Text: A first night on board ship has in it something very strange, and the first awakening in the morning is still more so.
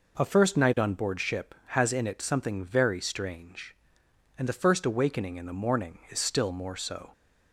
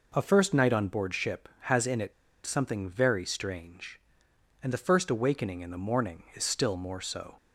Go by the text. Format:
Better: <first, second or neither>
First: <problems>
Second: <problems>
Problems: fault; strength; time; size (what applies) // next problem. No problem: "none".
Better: first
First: none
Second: pauses between "it" and "something"; slight; at 2.1 s; 0.32 s long